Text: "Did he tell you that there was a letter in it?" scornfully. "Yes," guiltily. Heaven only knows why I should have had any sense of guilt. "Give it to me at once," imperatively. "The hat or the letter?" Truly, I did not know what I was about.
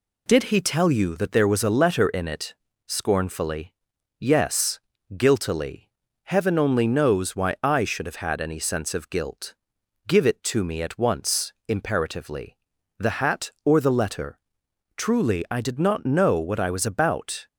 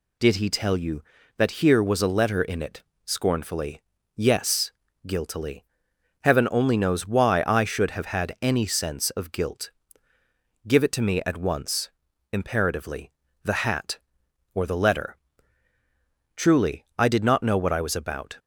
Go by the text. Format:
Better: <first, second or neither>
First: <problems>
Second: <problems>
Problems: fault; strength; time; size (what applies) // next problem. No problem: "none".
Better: first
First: none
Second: says "here" for "there"; at 1.6 s